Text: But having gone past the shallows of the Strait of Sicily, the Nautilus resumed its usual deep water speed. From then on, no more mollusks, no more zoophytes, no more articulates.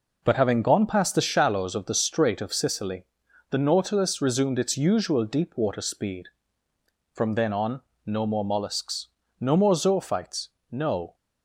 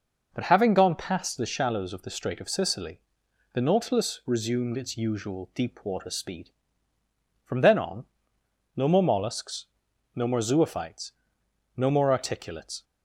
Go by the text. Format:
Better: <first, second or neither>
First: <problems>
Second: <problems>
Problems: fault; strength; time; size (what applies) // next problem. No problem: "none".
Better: second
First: stops before "more articulates"; at 11.1 s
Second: none